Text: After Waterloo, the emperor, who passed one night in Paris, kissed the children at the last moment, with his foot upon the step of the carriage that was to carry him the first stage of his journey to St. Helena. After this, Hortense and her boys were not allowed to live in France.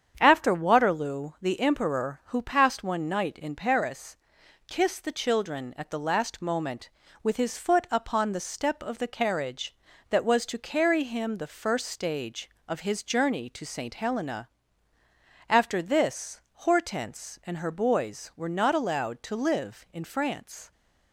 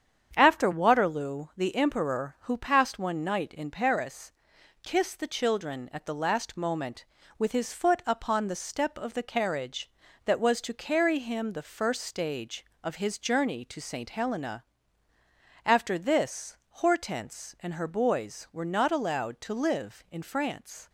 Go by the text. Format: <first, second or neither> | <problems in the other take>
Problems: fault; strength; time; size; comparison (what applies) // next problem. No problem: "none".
neither | starts louder than the rest; strong; the same in both